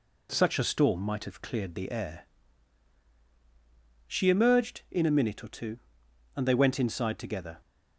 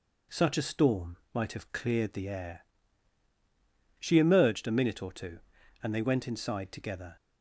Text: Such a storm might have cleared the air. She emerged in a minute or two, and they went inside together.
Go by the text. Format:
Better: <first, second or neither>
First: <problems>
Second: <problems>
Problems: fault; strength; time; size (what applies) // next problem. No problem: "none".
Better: first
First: none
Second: pauses between "storm" and "might"; slight; at 1.1 s; 0.18 s long // skips "in"; at 4.6 s